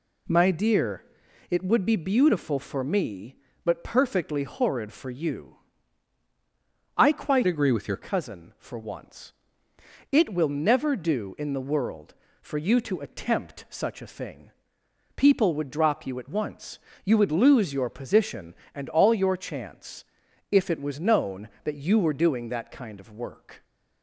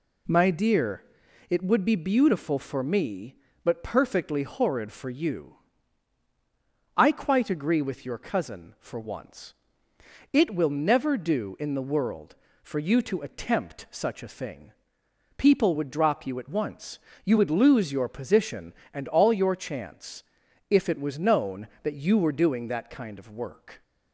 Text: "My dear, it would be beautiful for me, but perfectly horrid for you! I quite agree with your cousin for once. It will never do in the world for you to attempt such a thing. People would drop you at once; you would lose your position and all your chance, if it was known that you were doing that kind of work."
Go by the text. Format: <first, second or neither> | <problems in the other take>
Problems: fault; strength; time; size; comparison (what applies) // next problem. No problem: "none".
second | changes voice from "agree" to "your"; from 7.4 to 7.9 s; 0.5 s long